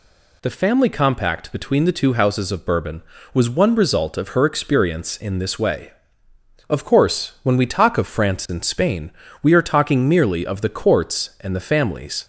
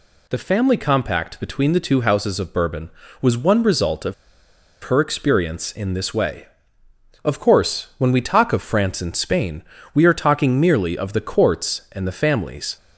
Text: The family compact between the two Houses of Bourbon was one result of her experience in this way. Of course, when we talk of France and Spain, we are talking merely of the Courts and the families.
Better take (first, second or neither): first